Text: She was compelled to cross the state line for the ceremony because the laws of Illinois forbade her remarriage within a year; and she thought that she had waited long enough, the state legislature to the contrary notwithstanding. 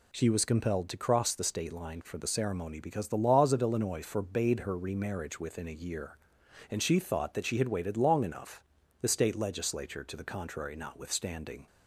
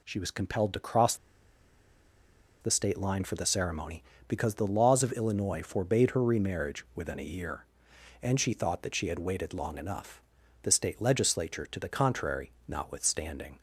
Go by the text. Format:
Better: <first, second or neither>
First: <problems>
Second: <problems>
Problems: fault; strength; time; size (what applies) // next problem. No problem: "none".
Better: first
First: none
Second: pauses between "cross" and "the"; strong; at 1.1 s; 1.4 s long // pauses between "contrary" and "notwithstanding"; slight; at 12.4 s; 0.16 s long